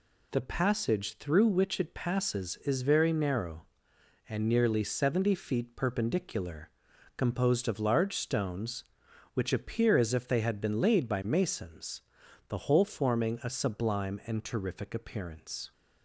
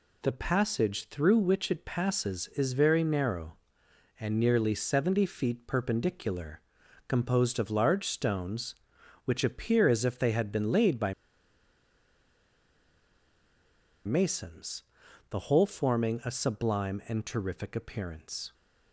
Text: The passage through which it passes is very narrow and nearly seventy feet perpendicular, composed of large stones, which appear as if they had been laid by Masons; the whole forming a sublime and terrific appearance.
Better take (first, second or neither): first